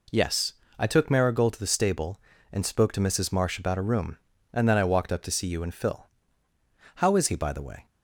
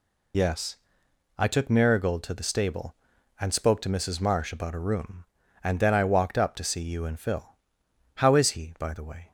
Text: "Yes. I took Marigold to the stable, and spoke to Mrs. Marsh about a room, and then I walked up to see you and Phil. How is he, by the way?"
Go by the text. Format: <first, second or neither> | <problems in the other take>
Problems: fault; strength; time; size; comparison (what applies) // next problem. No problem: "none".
first | loses the start of "Yes"; at 0.3 s; 105 ms